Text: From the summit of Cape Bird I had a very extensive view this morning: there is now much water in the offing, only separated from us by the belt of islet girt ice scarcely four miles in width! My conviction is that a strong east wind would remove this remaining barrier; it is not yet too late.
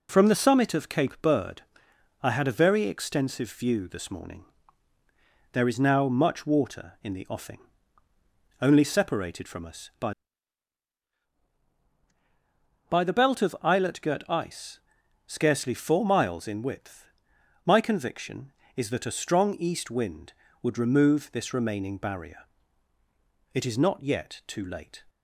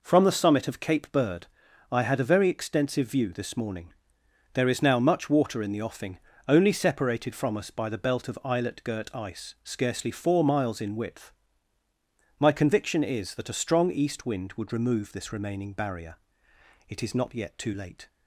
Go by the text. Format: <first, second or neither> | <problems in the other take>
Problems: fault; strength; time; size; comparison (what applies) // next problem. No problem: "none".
second | pauses between "Bird" and "I"; noticeable; at 1.6 s; 0.58 s long; noticeable in the second // says "by" twice; at 12.8 s // pauses between "ice" and "scarcely"; noticeable; at 14.8 s; 0.48 s long